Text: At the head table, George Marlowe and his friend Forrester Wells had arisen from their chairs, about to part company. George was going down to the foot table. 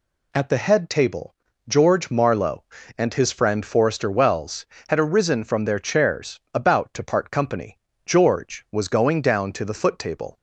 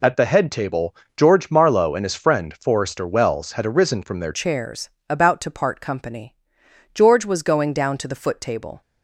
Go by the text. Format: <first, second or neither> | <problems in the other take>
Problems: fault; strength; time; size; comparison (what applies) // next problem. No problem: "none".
first | changes voice at "chairs"; from 4.3 s on; 4.5 s long